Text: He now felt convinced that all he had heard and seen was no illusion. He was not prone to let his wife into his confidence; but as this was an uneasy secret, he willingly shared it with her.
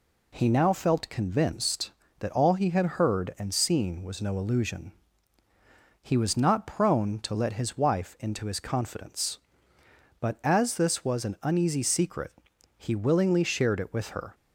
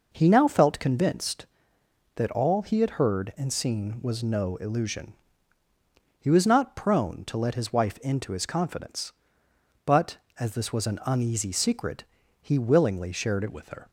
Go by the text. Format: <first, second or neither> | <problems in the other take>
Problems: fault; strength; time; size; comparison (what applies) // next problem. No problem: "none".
first | changes voice at "with"; from 13.5 s on; 0.3 s long